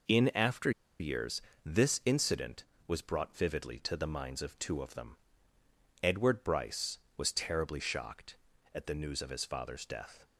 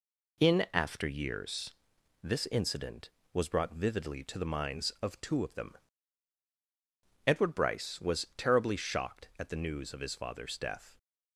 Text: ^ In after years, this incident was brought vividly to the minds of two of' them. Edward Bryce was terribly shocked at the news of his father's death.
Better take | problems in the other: second | pauses between "after" and "years"; slight; at 0.7 s; 0.29 s long

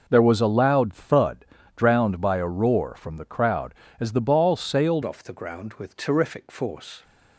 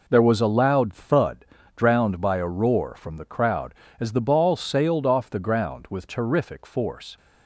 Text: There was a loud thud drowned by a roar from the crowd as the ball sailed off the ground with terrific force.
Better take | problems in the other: second | pauses between "thud" and "drowned"; slight; at 1.4 s; 0.30 s long; slight in the second // changes voice at "off"; from 5.0 s on; 2.0 s long

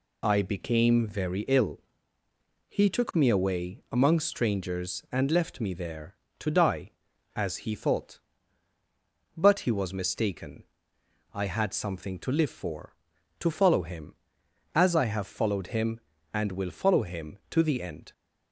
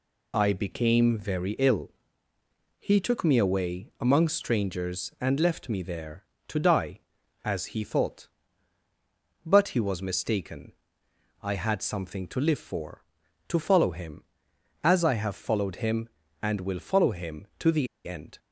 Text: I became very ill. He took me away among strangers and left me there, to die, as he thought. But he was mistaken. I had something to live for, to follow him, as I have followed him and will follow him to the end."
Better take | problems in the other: first | pauses between "the" and "end"; slight; at 17.8 s; 0.19 s long

